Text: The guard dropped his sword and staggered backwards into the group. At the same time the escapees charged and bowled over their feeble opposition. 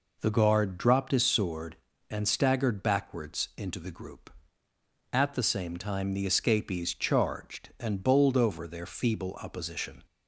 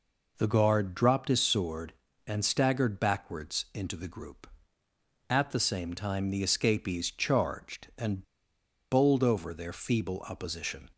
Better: first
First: none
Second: pauses between "and" and "bowled"; noticeable; at 8.2 s; 0.68 s long

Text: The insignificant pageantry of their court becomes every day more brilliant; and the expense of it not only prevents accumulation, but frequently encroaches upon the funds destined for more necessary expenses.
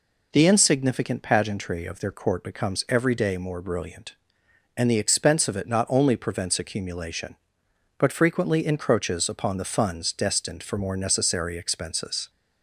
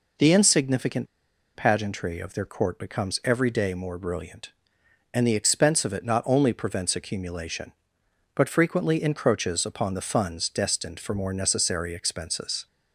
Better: first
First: none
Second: pauses between "insignificant" and "pageantry"; noticeable; at 1.0 s; 0.49 s long

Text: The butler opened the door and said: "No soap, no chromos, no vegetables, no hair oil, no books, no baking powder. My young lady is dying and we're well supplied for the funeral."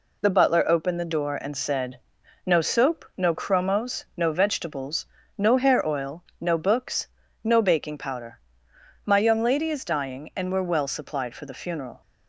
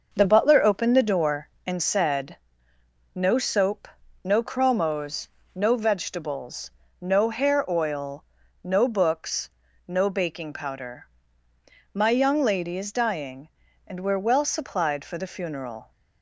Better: first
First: none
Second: starts louder than the rest; noticeable; until 1.8 s; 6 dB

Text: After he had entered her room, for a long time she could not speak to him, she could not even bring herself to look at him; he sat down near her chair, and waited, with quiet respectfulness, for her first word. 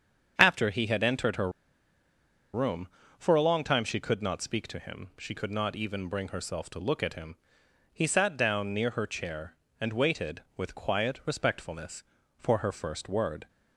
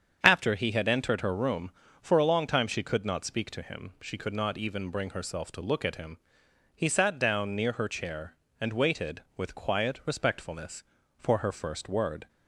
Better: second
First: starts louder than the rest; strong; until 1.3 s; 8 dB // pauses between "her" and "room"; at 1.4 s; 1.0 s long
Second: starts louder than the rest; strong; until 1.2 s; 7.5 dB

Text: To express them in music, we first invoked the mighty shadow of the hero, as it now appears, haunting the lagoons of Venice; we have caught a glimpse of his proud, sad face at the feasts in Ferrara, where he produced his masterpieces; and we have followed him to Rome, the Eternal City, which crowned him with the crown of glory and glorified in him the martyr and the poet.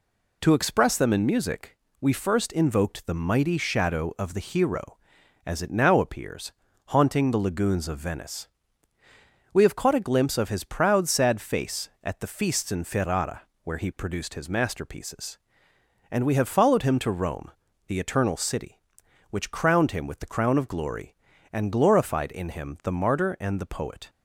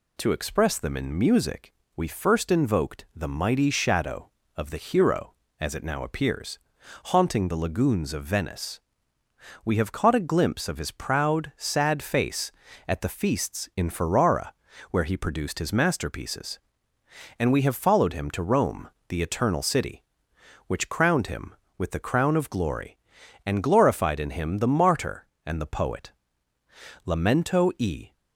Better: first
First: none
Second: goes on to say "Lamento e"; noticeable; from 27.0 s on; 1.0 s long

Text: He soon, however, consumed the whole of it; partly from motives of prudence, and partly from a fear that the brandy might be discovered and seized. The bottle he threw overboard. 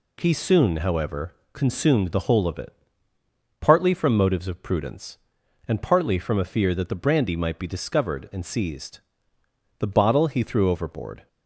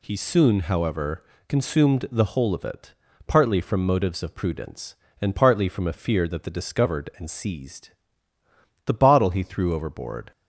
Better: first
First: none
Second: skips "brandy might be"; at 6.5 s

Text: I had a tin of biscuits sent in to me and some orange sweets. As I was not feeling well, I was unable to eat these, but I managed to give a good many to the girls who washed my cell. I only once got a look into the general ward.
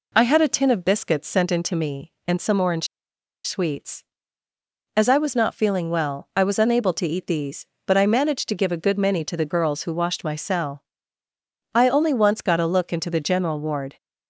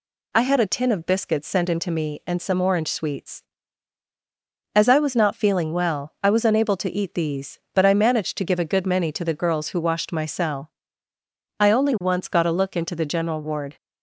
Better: second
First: pauses between "orange" and "sweets"; noticeable; at 2.8 s; 0.57 s long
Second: none

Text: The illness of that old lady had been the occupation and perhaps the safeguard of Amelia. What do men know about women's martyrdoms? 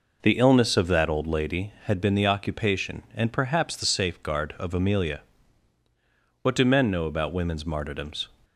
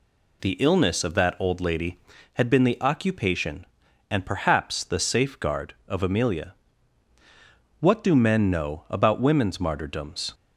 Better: second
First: starts louder than the rest; noticeable; until 1.4 s; 5 dB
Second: none

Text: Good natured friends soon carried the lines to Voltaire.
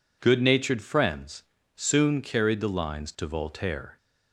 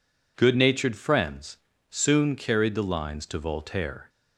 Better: neither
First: pauses between "friends" and "soon"; slight; at 1.4 s; 0.32 s long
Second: pauses between "friends" and "soon"; slight; at 1.5 s; 0.32 s long

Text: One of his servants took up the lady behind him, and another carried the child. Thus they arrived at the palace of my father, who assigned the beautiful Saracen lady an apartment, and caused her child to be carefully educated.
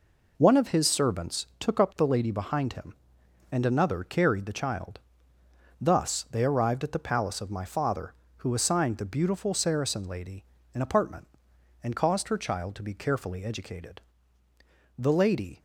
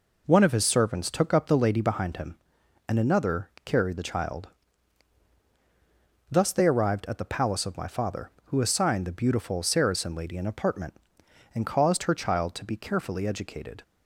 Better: second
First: pauses between "lady" and "an"; slight; at 10.4 s; 0.30 s long // goes on to say "The lady"; noticeable; from 14.9 s on; 0.64 s long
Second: none

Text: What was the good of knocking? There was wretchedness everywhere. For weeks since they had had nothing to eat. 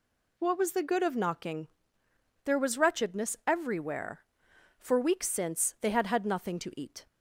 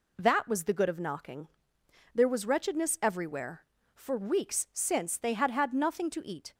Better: first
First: none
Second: says "That" for "What"; at 0.1 s

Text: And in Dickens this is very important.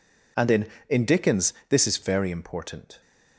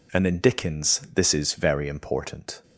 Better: second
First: says "in" twice; at 0.8 s // pauses between "Dickens" and "this"; slight; at 1.5 s; 0.16 s long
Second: none

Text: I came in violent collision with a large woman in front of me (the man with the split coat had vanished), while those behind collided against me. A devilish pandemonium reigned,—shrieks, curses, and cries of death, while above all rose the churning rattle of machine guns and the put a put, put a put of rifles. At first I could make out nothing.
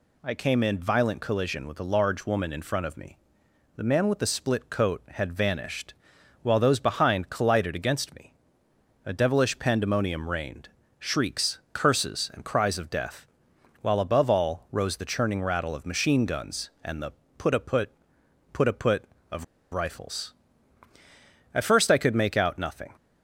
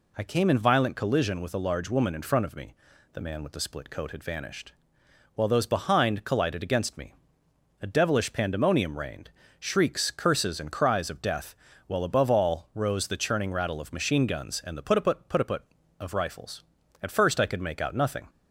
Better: second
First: pauses between "the" and "put"; slight; at 17.1 s; 0.26 s long // pauses between "of" and "rifles"; slight; at 19.4 s; 0.27 s long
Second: none

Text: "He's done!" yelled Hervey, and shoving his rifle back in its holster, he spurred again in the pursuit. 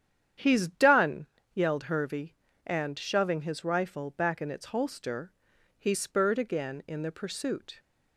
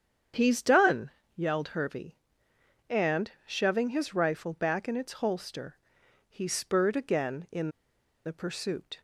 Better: first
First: starts louder than the rest; strong; until 1.6 s; 9.5 dB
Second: starts louder than the rest; strong; until 1.6 s; 8 dB // pauses between "and" and "shoving"; slight; at 3.3 s; 0.16 s long // pauses between "in" and "the"; noticeable; at 7.6 s; 0.56 s long

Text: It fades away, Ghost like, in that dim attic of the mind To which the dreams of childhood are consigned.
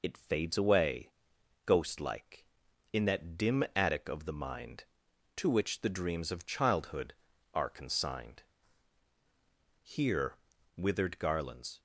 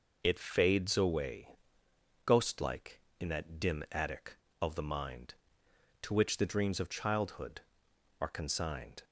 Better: second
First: goes on to say "Here withered garlands"; strong; from 9.8 s on; 1.9 s long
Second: none

